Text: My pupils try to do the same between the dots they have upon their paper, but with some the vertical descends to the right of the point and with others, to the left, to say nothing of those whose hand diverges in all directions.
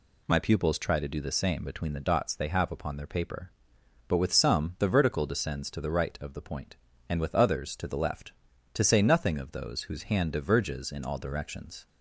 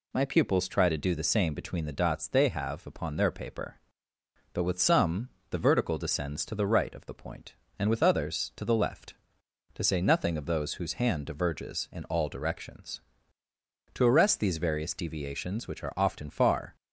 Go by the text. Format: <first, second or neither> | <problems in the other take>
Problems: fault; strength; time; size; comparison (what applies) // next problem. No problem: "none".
first | pauses between "some" and "the"; slight; at 5.2 s; 0.20 s long // goes on to say "To arrest these various deviations which are often far"; strong; from 13.9 s on; 2.8 s long